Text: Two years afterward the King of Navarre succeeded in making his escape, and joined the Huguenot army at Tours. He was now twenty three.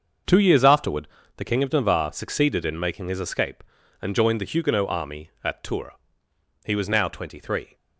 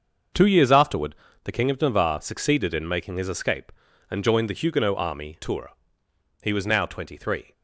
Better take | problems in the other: first | starts louder than the rest; until 1.6 s; 6.5 dB; also in the first // pauses between "afterward" and "the"; slight; at 1.1 s; 0.30 s long; slight in the first // skips "at"; at 5.3 s

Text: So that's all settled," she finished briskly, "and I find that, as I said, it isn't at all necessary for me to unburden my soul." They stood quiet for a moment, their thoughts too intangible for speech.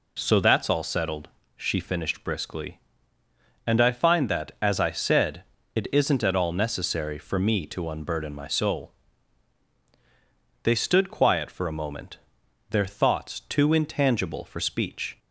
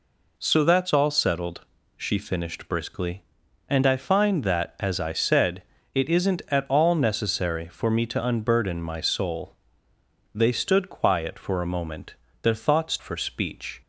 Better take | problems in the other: first | skips "too intangible"; at 12.9 s

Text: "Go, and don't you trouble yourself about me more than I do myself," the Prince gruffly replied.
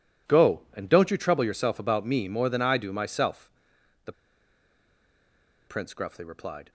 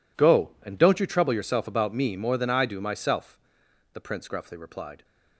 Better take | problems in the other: second | pauses between "the" and "Prince"; strong; at 4.1 s; 1.5 s long

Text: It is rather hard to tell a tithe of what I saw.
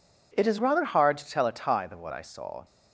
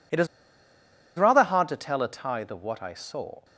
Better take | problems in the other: first | pauses between "is" and "rather"; noticeable; at 0.2 s; 0.91 s long

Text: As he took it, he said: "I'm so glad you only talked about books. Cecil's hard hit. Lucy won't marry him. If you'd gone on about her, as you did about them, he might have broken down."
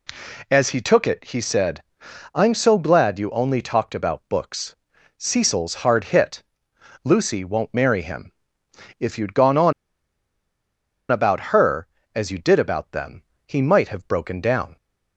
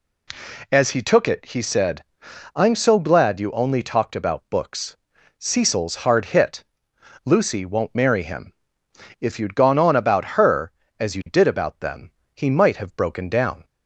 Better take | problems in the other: second | pauses between "on" and "about"; strong; at 9.7 s; 1.3 s long

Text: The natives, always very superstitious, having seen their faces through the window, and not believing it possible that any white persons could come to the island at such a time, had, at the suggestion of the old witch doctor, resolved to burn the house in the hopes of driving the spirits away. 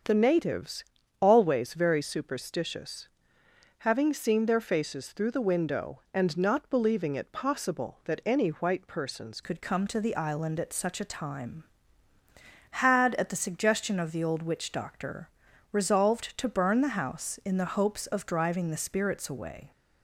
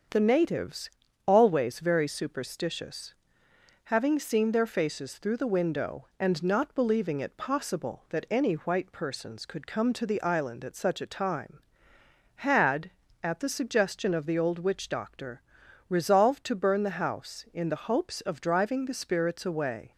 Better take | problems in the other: second | starts louder than the rest; until 1.4 s; 7 dB; also in the second // changes voice at "could"; from 9.4 s on; 10.3 s long

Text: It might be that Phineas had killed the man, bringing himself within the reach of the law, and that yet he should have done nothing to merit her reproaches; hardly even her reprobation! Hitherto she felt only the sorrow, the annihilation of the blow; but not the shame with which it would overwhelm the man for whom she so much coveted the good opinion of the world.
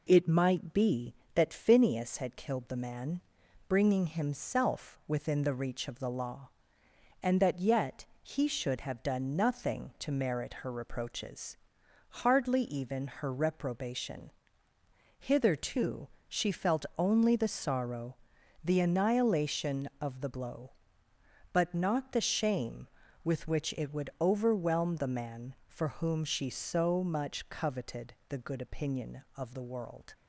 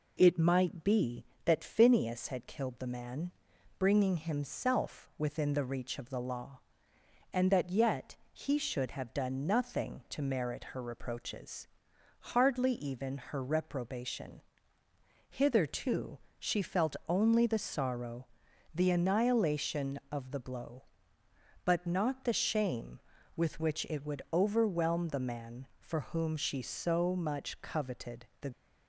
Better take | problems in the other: first | pauses between "yet" and "he"; slight; at 8.1 s; 0.16 s long; slight in the first // pauses between "Hitherto" and "she"; slight; at 16.1 s; 0.22 s long; slight in the first // pauses between "coveted" and "the"; slight; at 28.2 s; 0.16 s long; slight in the first // stops before "good opinion of the world"; at 28.5 s

